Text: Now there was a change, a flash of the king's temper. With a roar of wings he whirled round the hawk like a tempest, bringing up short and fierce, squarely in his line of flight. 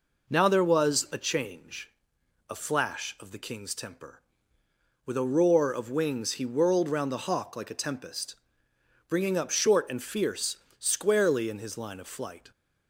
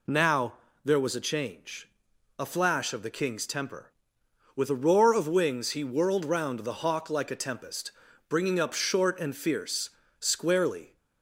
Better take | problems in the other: first | pauses between "Now" and "there"; slight; at 0.5 s; 0.32 s long // stops before "in his line of flight"; at 10.9 s

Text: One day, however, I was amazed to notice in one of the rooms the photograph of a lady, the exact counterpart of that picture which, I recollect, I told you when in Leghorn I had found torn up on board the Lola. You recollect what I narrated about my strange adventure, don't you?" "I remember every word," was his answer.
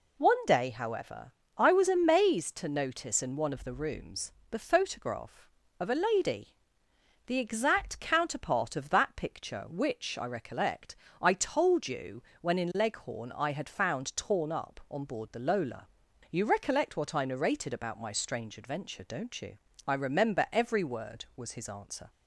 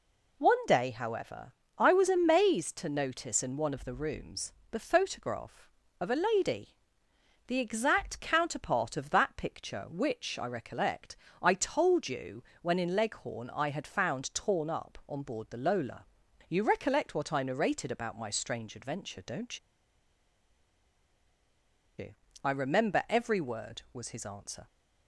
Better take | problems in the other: first | pauses between "rooms" and "the"; slight; at 4.5 s; 0.20 s long; slight in the first // pauses between "you" and "when"; slight; at 12.4 s; 0.20 s long; slight in the first // pauses between "don't" and "you"; strong; at 19.5 s; 2.3 s long

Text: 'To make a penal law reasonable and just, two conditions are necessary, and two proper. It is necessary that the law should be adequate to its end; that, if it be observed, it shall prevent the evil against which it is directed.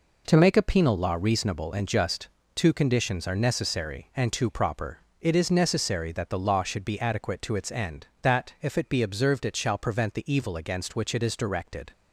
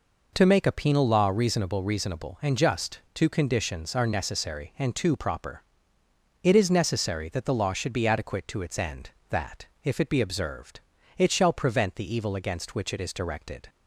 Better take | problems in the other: first | says "reasonable" twice; at 1.8 s

